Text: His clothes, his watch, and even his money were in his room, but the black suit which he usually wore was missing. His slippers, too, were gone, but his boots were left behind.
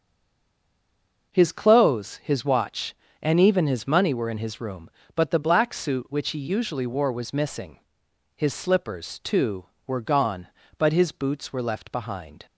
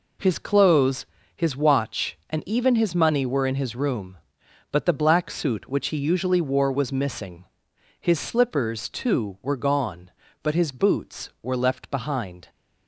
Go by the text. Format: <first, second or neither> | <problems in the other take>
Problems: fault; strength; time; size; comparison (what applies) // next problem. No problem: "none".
second | stays silent before the first word; noticeable; until 1.3 s; 1.3 s long